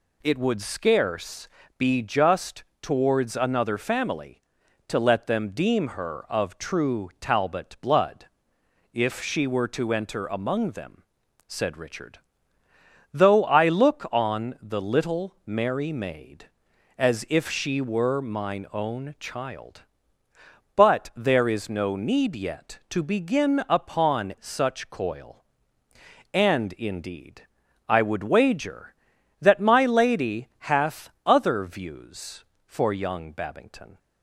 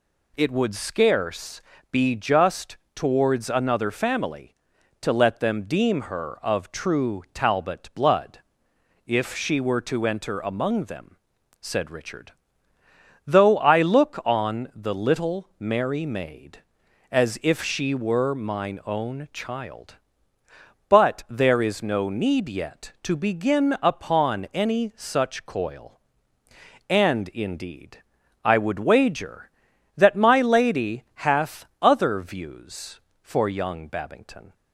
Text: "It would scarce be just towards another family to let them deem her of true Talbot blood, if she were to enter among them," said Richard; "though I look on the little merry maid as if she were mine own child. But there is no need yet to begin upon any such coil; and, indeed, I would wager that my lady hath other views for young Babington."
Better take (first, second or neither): second